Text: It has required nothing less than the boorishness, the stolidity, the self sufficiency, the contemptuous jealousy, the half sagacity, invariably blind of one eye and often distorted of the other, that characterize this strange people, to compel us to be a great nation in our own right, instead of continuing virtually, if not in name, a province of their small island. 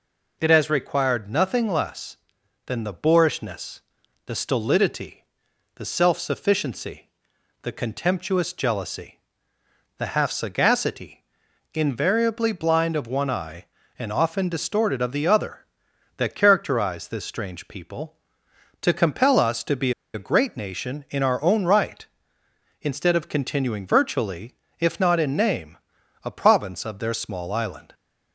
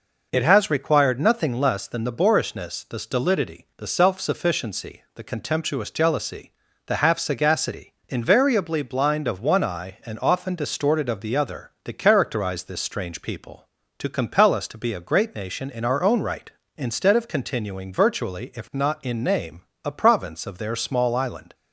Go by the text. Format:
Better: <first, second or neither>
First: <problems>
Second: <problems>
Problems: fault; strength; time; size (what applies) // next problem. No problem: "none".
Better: second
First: pauses between "be" and "a"; slight; at 19.9 s; 0.23 s long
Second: none